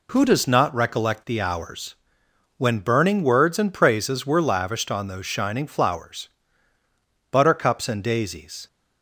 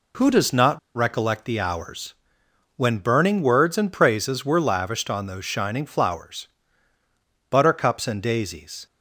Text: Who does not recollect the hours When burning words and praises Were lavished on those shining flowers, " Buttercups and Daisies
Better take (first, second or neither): first